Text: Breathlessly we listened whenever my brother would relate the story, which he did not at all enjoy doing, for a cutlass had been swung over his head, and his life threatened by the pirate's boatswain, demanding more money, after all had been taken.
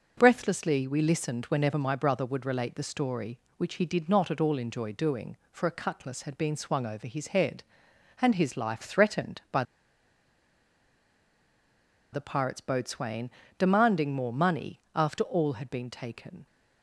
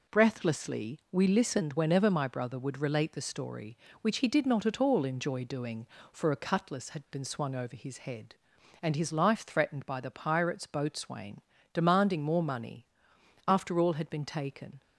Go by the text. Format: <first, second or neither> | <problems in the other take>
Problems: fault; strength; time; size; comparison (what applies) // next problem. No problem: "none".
second | pauses between "by" and "the"; strong; at 9.6 s; 2.5 s long